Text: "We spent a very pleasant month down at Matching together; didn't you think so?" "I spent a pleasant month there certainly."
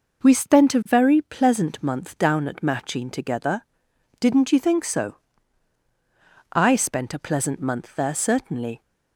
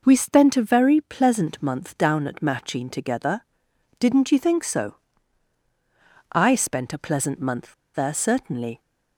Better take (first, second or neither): first